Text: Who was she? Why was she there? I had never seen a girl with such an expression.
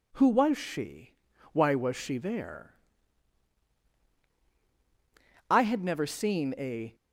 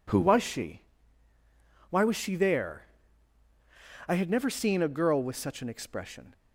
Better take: second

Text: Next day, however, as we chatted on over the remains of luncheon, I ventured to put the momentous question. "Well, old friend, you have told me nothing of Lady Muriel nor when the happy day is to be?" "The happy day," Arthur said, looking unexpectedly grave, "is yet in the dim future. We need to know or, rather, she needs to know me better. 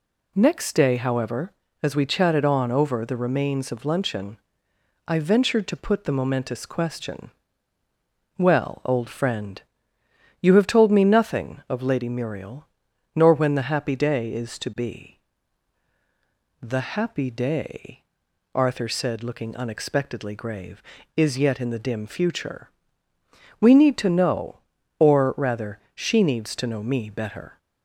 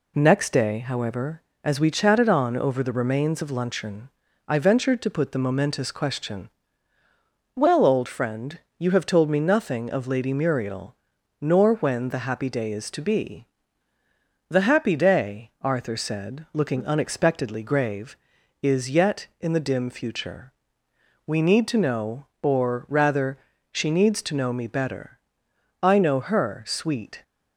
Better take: first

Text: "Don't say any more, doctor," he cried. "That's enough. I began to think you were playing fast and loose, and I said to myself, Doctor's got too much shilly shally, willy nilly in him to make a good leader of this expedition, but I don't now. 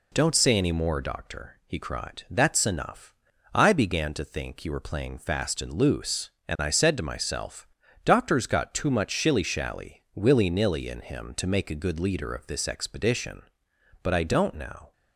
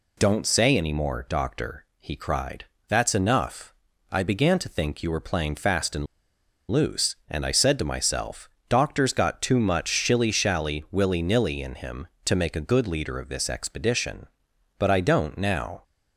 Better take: first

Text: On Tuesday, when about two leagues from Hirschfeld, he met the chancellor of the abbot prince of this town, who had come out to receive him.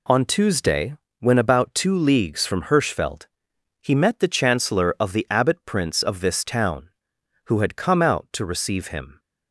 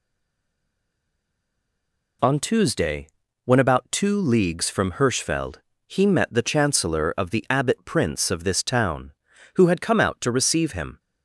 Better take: first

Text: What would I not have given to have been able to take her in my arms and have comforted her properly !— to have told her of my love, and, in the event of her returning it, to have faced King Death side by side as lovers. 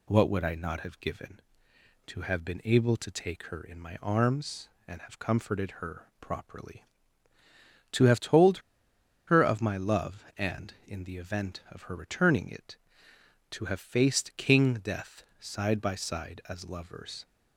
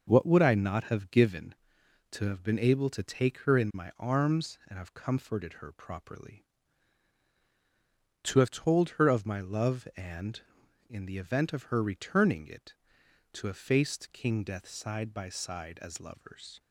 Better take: second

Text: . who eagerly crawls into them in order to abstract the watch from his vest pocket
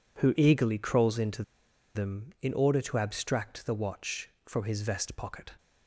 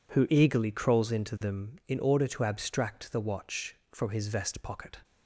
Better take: second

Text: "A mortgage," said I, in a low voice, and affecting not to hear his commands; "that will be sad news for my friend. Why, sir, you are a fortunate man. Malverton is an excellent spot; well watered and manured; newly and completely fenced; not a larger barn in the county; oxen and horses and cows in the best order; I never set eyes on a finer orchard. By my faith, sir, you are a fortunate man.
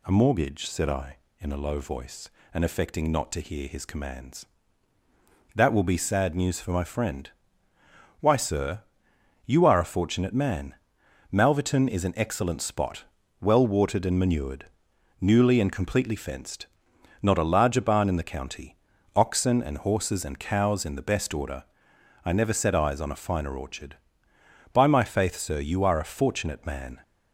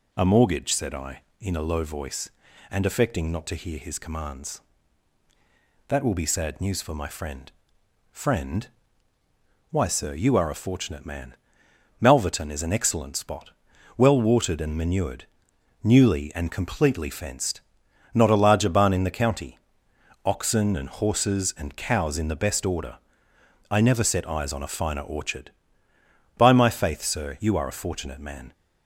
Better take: first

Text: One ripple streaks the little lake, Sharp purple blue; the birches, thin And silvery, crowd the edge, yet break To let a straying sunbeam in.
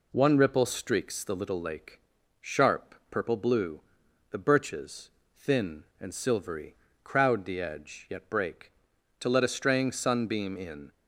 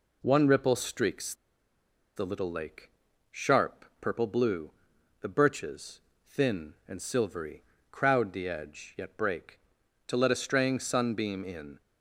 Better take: first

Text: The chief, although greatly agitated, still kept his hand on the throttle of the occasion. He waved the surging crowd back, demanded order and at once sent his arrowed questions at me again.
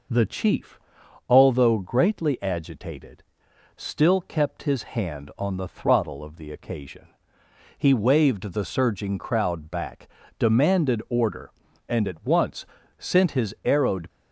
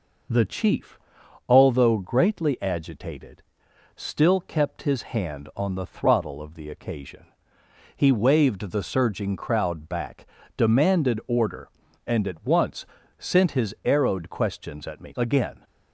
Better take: second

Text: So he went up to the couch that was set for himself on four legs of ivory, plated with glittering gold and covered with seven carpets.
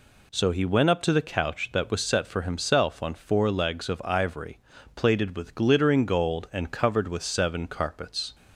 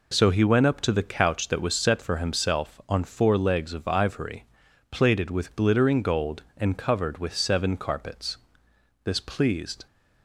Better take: first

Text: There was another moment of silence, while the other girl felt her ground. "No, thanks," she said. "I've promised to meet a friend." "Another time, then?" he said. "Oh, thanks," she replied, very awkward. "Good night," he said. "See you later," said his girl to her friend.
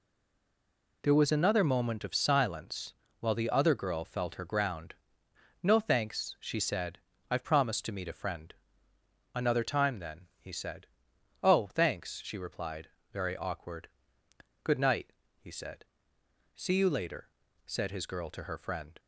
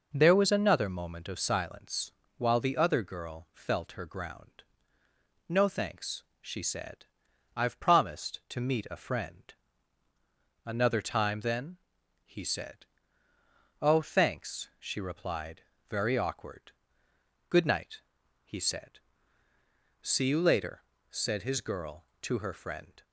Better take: second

